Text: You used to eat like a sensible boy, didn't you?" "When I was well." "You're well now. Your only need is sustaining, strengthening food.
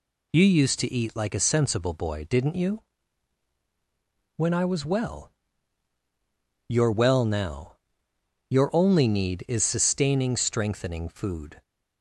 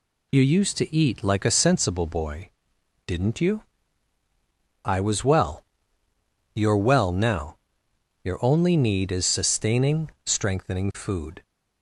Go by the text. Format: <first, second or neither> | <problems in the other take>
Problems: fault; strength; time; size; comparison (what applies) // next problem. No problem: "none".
first | skips "When"; at 4.2 s